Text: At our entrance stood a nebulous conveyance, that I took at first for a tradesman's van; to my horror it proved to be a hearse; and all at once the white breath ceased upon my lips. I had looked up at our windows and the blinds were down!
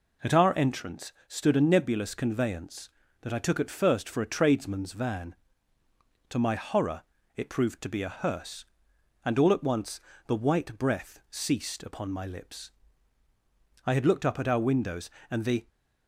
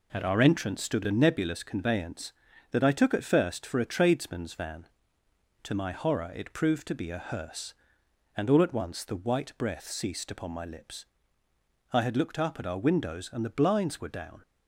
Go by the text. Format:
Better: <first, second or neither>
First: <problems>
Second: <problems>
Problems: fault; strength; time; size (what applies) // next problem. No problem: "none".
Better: second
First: pauses between "entrance" and "stood"; slight; at 1.1 s; 0.16 s long // pauses between "horror" and "it"; slight; at 7.0 s; 0.34 s long // pauses between "once" and "the"; slight; at 10.0 s; 0.26 s long // stops before "blinds were down"; at 15.6 s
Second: none